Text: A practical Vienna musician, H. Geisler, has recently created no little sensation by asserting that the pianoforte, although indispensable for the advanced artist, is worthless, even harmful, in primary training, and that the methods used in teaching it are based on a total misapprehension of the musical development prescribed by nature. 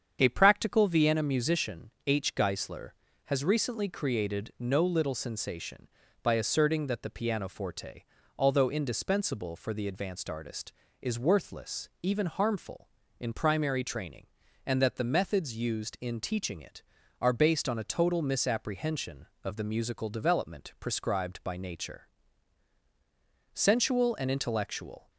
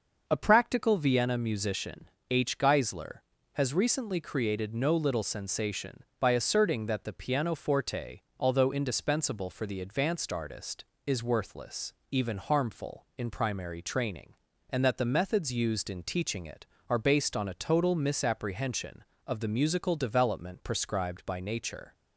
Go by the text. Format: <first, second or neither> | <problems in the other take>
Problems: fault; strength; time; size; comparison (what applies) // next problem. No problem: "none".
second | starts louder than the rest; strong; until 1.2 s; 7.5 dB // goes on to say "Sensual and intellectual"; from 23.5 s on; 1.5 s long